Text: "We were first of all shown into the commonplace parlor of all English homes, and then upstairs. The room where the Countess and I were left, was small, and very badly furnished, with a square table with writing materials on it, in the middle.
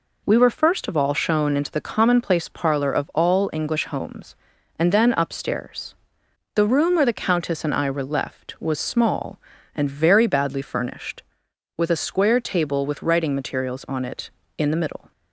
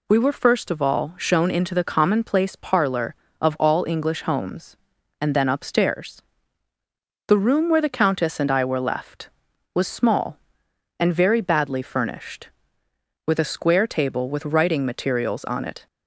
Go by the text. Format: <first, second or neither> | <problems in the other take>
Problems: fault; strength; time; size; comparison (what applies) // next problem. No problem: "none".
first | stops before "in the middle"; at 15.8 s